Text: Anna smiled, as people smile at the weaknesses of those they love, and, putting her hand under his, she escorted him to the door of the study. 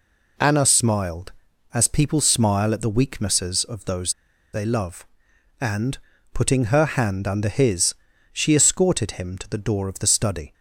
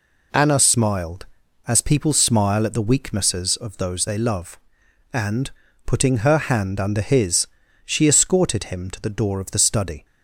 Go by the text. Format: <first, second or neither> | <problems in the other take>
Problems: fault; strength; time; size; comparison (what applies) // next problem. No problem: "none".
second | pauses between "those" and "they"; at 4.1 s; 0.41 s long